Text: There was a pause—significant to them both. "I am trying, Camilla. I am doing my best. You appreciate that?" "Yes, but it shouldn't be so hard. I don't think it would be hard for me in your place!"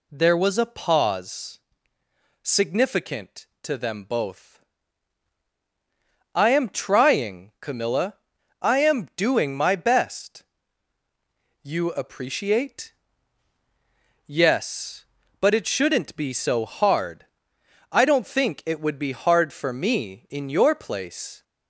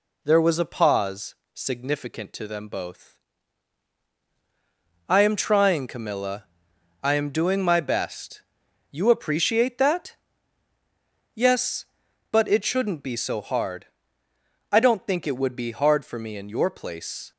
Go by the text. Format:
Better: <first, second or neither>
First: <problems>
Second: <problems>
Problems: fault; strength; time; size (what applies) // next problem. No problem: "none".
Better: second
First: skips "that"; at 13.5 s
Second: none